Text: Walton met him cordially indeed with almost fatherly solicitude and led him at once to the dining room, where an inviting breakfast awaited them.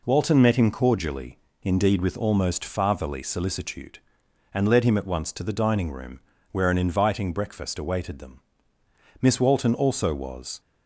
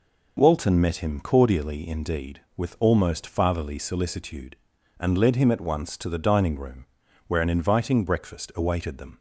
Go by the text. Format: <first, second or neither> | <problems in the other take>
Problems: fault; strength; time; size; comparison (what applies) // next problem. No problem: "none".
second | pauses between "cordially" and "indeed"; slight; at 1.3 s; 0.28 s long // goes on to say "Miss Walton also was"; from 9.2 s on; 1.3 s long